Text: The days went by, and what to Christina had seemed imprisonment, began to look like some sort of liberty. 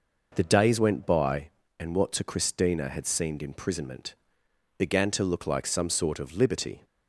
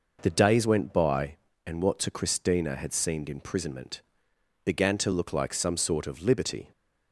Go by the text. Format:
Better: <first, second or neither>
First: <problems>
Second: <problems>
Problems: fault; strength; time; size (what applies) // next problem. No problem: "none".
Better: neither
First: none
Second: none